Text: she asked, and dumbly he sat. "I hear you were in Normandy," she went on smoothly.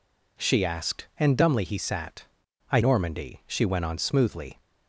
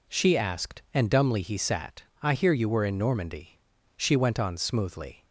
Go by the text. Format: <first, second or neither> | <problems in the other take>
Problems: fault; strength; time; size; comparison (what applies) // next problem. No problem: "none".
second | skips "hear you were in"; at 2.8 s